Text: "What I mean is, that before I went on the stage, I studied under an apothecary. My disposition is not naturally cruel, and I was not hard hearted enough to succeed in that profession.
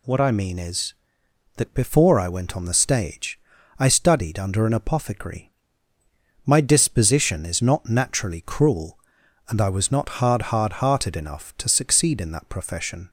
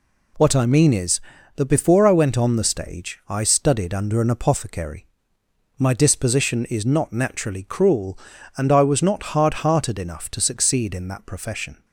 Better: second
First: says "hard" twice; at 10.5 s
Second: none

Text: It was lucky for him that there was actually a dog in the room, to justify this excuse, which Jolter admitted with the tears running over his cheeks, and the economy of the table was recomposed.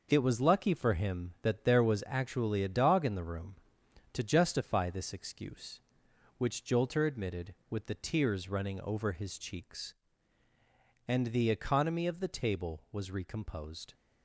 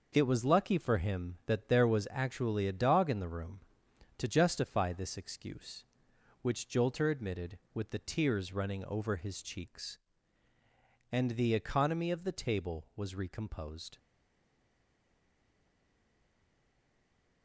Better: first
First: none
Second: stays silent after the last word; strong; from 13.9 s on; 3.5 s long

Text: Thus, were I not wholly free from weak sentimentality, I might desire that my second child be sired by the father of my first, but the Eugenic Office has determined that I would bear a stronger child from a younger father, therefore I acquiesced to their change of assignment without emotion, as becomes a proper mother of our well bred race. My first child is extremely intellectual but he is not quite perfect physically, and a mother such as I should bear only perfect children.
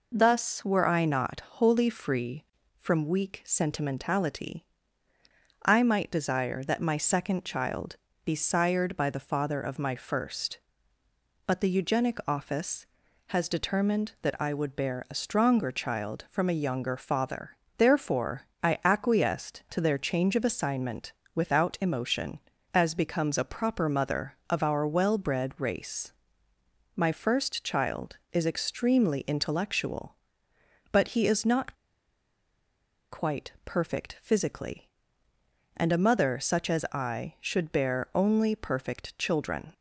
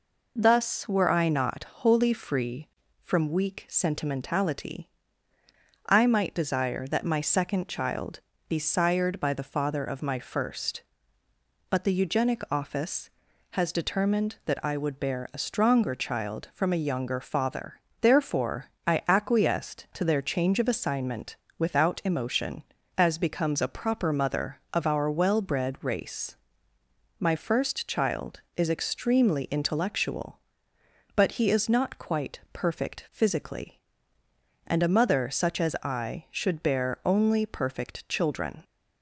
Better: second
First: pauses between "child" and "be"; slight; at 7.9 s; 0.28 s long // pauses between "therefore" and "I"; slight; at 18.4 s; 0.18 s long // pauses between "assignment" and "without"; slight; at 21.1 s; 0.22 s long // pauses between "not" and "quite"; strong; at 31.7 s; 1.3 s long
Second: pauses between "child" and "be"; slight; at 8.1 s; 0.28 s long // pauses between "therefore" and "I"; slight; at 18.6 s; 0.18 s long // pauses between "assignment" and "without"; slight; at 21.3 s; 0.22 s long

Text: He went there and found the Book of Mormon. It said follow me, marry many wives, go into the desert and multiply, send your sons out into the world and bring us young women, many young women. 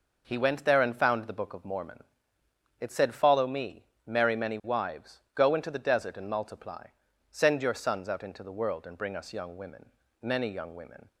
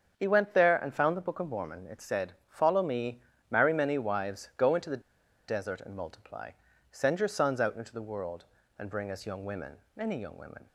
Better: first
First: none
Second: starts louder than the rest; strong; until 1.1 s; 7 dB // pauses between "said" and "follow"; slight; at 2.3 s; 0.16 s long // pauses between "the" and "desert"; noticeable; at 5.0 s; 0.47 s long

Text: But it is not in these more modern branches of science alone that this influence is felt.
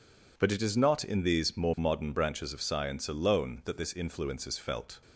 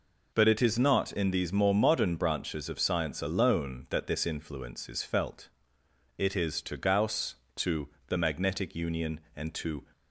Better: first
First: none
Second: goes on to say "It is to Gauss to the Magnetic Union and to"; strong; from 6.1 s on; 3.6 s long

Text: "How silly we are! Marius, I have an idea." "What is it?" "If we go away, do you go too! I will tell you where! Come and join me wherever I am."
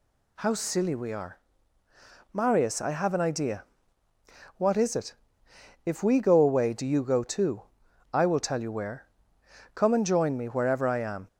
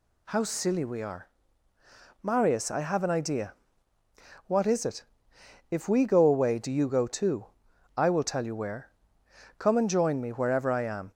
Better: neither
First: none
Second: none

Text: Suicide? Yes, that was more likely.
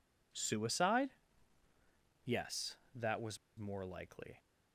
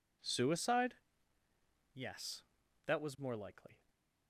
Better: second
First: pauses between "was" and "more"; slight; at 3.3 s; 0.20 s long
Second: none

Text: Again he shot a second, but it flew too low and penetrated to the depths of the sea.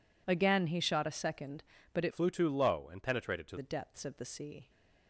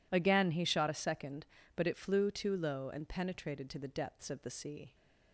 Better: second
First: changes voice from "flew" to "to"; from 2.1 to 3.5 s; 1.4 s long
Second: none

